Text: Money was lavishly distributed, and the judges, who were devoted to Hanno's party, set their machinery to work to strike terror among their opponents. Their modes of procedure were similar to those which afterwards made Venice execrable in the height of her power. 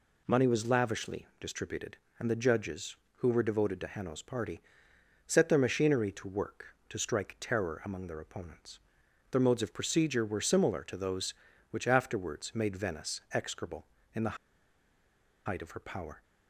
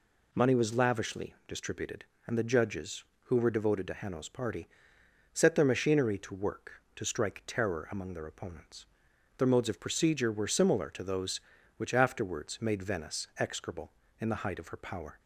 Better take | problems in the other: second | pauses between "the" and "height"; at 14.3 s; 1.0 s long

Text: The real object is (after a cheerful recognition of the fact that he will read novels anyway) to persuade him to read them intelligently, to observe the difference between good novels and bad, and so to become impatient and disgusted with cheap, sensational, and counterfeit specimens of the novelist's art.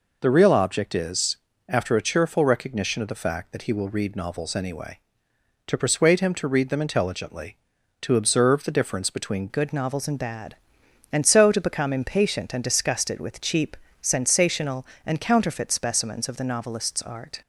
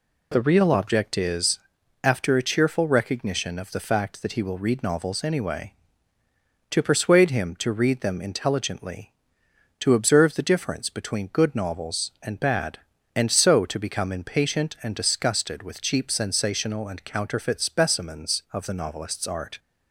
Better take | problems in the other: second | changes voice at "good"; from 9.4 s on; 8.0 s long

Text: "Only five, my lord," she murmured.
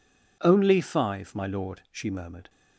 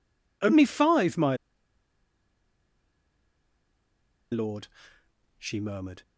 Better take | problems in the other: first | pauses between "my" and "lord"; strong; at 1.3 s; 2.9 s long

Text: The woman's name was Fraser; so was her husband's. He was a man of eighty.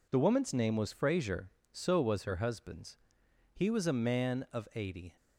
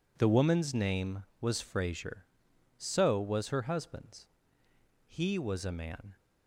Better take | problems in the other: first | stops before "of eighty"; at 6.1 s

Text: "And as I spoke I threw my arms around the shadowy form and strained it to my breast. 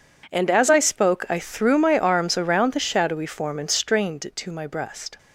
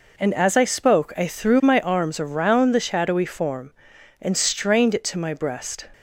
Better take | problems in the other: neither | none

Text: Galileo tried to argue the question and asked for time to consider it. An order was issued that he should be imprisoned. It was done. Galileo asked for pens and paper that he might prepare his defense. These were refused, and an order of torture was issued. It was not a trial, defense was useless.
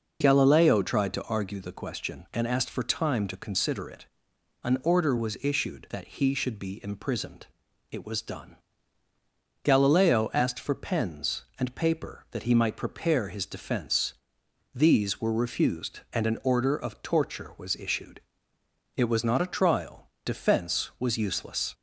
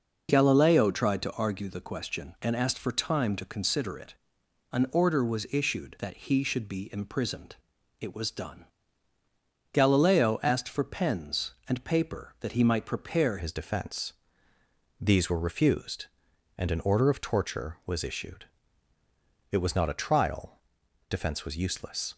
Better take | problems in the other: first | changes voice at "his"; from 13.3 s on; 8.8 s long

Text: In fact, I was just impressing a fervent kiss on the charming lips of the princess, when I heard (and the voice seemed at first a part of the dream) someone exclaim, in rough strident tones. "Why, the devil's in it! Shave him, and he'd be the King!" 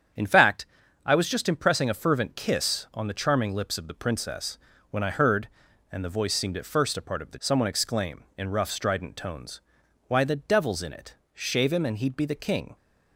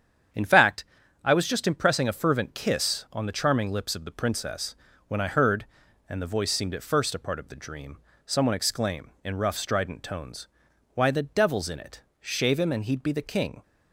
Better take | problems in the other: second | starts louder than the rest; strong; until 1.5 s; 8 dB; strong in the second // skips "dream"; at 7.3 s

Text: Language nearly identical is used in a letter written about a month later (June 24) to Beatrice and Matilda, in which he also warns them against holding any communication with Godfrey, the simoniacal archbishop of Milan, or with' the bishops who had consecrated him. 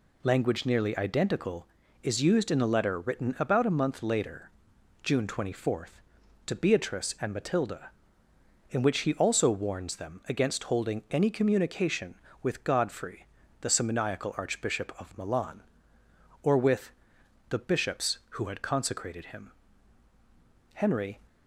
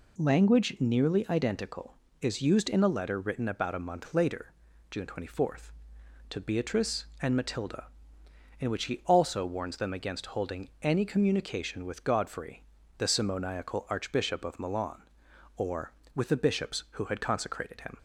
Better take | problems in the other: second | pauses between "with" and "the"; noticeable; at 16.9 s; 0.60 s long // goes on to say "Henry"; slight; from 20.7 s on; 0.46 s long

